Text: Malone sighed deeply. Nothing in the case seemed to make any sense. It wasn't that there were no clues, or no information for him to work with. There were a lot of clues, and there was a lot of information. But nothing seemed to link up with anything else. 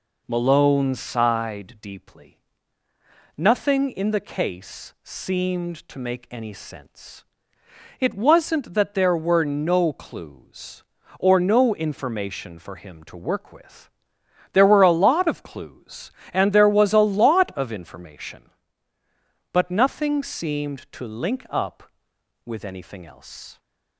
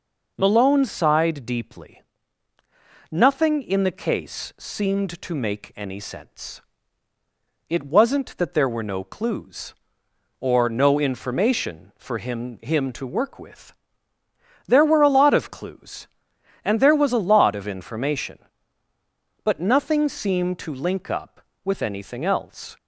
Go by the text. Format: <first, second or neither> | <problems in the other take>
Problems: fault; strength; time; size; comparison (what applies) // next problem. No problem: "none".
first | says "him" twice; at 12.6 s